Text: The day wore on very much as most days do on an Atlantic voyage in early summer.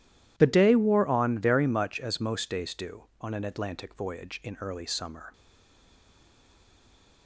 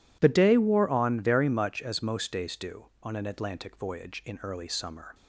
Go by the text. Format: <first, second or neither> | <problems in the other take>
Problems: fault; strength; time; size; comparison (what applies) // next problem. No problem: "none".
second | stays silent after the last word; noticeable; from 5.3 s on; 1.9 s long